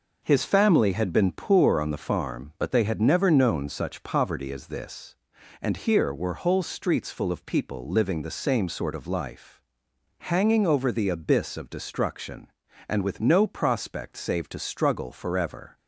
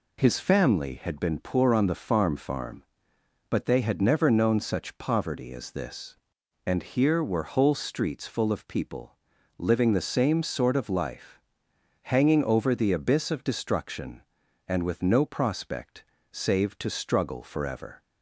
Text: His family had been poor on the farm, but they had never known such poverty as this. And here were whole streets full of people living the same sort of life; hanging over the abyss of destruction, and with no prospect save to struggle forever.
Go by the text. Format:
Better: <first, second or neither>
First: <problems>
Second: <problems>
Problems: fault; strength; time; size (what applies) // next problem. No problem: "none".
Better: first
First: none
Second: says "farm" twice; at 2.3 s // pauses between "people" and "living"; at 9.1 s; 0.42 s long // pauses between "prospect" and "save"; slight; at 16.0 s; 0.30 s long